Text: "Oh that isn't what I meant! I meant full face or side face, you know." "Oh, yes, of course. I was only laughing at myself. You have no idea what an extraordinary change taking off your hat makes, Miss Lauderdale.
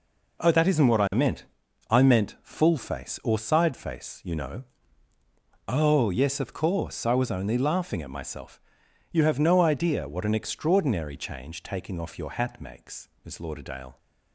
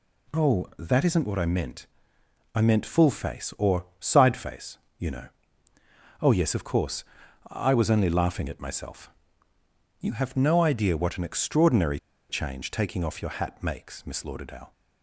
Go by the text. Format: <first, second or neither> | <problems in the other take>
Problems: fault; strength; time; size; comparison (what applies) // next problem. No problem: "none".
first | pauses between "extraordinary" and "change"; slight; at 11.9 s; 0.30 s long